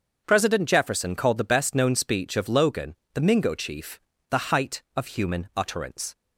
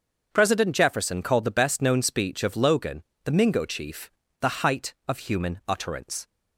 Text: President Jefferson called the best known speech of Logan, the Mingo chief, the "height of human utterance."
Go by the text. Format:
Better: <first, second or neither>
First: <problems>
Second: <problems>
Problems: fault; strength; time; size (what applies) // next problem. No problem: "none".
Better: neither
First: starts louder than the rest; until 1.2 s; 6.5 dB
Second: starts louder than the rest; until 1.3 s; 6.5 dB